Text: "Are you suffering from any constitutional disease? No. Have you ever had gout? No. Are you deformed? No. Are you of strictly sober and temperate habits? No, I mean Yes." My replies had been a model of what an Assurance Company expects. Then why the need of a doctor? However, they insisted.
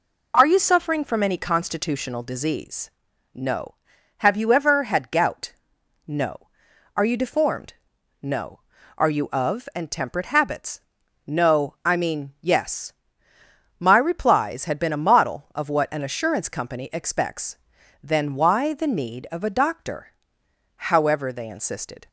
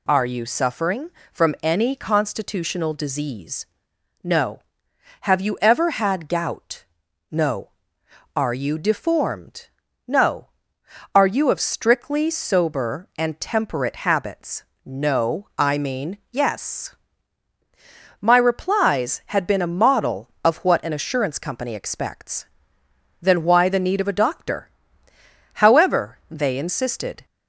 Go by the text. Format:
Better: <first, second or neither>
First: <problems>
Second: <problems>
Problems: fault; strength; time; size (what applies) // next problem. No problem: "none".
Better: second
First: skips "strictly sober"; at 9.7 s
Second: none